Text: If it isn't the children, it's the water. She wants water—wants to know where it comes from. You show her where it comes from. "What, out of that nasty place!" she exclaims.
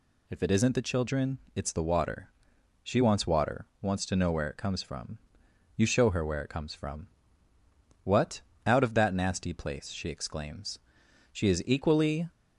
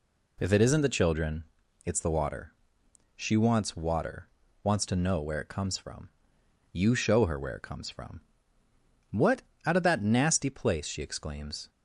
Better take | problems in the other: second | goes on to say "She is equally"; noticeable; from 11.3 s on; 0.96 s long

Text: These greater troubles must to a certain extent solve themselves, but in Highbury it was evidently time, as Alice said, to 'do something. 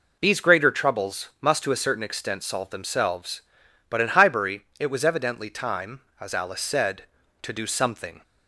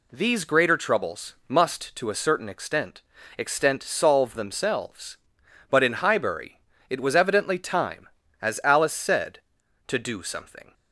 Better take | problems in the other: first | says "extent" twice; at 3.3 s // pauses between "Highbury" and "it"; slight; at 6.6 s; 0.28 s long; slight in the first

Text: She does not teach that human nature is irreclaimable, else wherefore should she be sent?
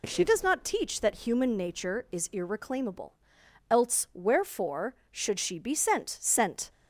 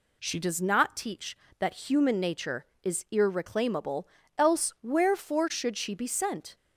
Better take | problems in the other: second | says "sent" twice; at 6.1 s

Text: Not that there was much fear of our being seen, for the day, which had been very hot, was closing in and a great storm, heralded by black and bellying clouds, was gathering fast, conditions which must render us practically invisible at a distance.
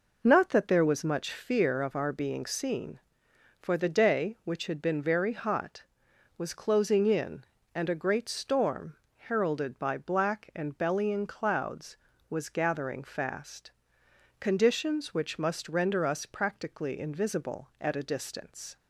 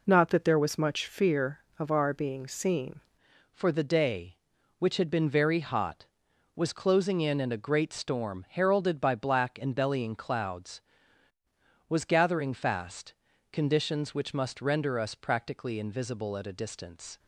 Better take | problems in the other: first | changes voice at "for"; from 3.5 s on; 13.6 s long

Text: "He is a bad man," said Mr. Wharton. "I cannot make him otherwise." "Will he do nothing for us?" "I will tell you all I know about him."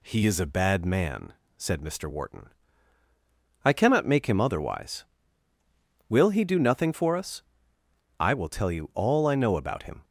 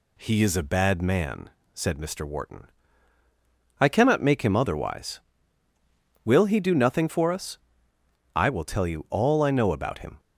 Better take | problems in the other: neither | none

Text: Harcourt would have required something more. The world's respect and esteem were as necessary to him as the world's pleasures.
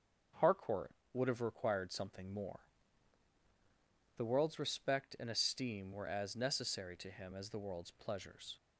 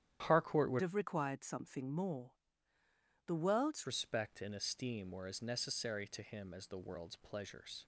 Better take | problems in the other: first | starts louder than the rest; strong; until 1.2 s; 10.5 dB; also in the first // changes voice from "have" to "world's"; from 0.8 to 3.8 s; 3.0 s long

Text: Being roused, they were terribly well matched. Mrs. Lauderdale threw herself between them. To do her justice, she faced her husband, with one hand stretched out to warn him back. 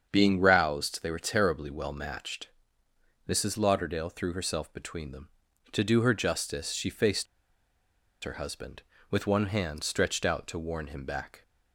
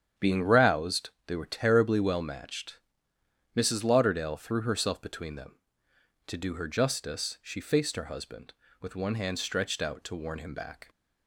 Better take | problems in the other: second | starts louder than the rest; strong; until 1.1 s; 7.5 dB; strong in the second // pauses between "faced" and "her"; at 7.2 s; 0.98 s long

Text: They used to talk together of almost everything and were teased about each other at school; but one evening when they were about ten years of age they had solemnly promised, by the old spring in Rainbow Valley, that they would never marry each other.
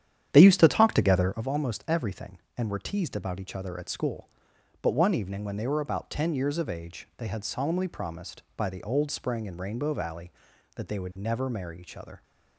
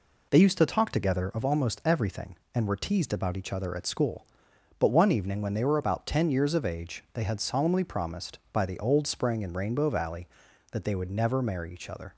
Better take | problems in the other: second | starts louder than the rest; strong; until 1.4 s; 10 dB

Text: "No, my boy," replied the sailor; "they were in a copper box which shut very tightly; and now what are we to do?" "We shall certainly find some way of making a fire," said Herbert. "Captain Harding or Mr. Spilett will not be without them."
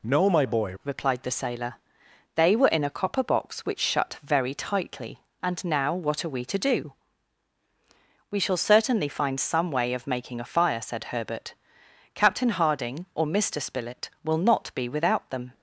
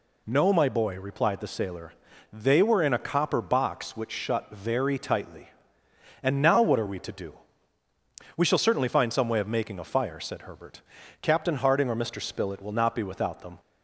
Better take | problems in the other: second | changes voice at "replied"; from 0.8 s on; 14.7 s long

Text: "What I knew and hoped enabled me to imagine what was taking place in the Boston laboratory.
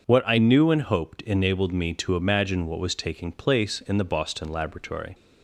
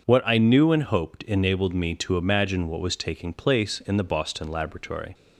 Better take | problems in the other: neither | starts louder than the rest; the same in both

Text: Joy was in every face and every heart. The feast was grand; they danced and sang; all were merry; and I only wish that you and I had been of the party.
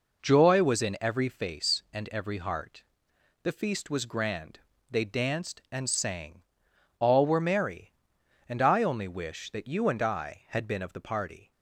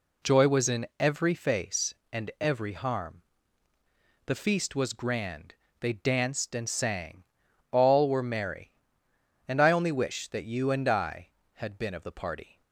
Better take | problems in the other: first | says "harm" for "heart"; at 2.7 s

